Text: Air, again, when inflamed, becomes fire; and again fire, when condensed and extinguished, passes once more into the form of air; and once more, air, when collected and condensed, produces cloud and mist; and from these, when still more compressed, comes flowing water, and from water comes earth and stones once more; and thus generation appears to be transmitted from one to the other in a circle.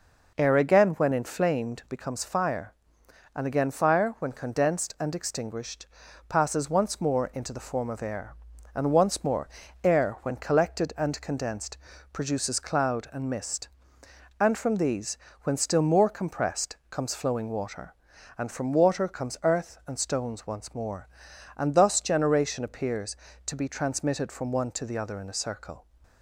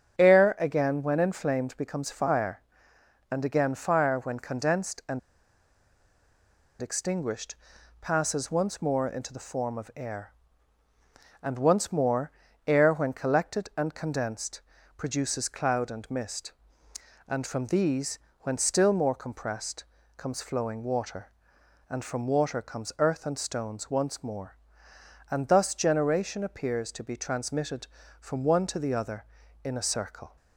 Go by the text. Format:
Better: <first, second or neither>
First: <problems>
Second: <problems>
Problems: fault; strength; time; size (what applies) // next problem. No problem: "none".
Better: first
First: none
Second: starts louder than the rest; strong; until 1.2 s; 8 dB // pauses between "and" and "extinguished"; strong; at 5.1 s; 1.6 s long